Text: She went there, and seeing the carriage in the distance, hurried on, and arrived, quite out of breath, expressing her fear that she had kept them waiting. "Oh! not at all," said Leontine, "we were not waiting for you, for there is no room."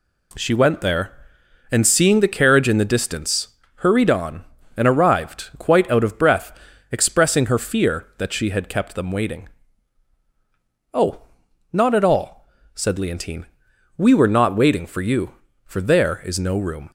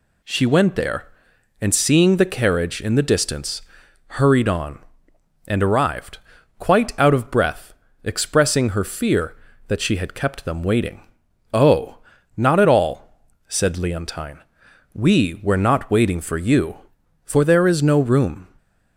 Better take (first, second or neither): neither